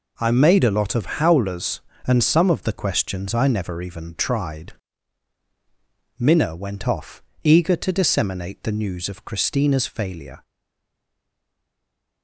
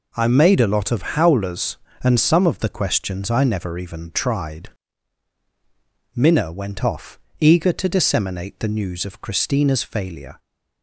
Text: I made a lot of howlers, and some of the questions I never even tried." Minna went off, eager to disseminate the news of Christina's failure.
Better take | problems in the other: second | stays silent after the last word; noticeable; from 10.4 s on; 1.8 s long

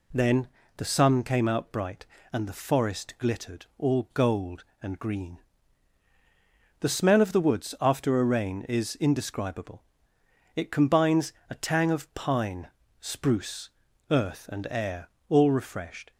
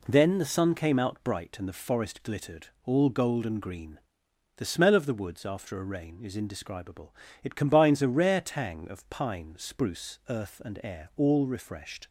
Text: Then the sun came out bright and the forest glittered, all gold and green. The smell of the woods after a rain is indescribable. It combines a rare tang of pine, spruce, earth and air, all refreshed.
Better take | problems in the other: second | pauses between "Then" and "the"; slight; at 0.4 s; 0.30 s long // pauses between "combines" and "a"; slight; at 11.3 s; 0.18 s long // skips "rare"; at 11.5 s

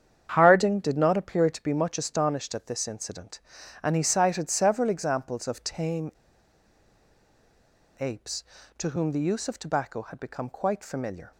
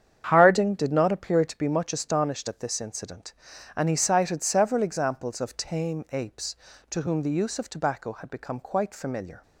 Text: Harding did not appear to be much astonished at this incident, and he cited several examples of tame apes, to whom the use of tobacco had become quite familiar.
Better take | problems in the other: second | starts louder than the rest; strong; until 1.3 s; 8.5 dB; strong in the second // pauses between "tame" and "apes"; strong; at 6.1 s; 1.8 s long

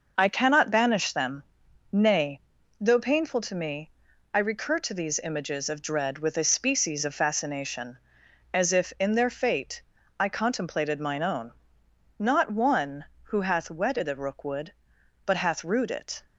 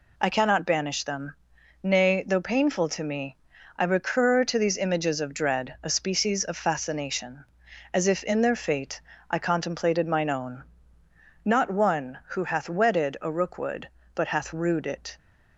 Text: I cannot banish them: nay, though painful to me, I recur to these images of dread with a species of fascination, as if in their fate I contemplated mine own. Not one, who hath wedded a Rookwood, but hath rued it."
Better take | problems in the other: first | skips "with"; at 5.7 s // pauses between "fate" and "I"; slight; at 9.0 s; 0.28 s long; slight in the first

